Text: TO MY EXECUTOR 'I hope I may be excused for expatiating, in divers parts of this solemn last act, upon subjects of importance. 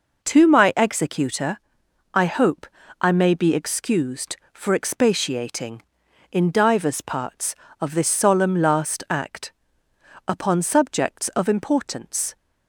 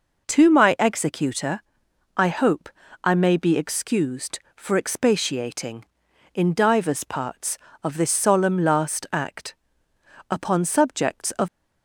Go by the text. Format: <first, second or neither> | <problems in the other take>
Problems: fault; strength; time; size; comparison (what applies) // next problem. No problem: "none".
first | pauses between "EXECUTOR" and "I"; noticeable; at 1.6 s; 0.56 s long; noticeable in the first // pauses between "hope" and "I"; slight; at 2.7 s; 0.34 s long; slight in the first // stops before "importance"; at 11.4 s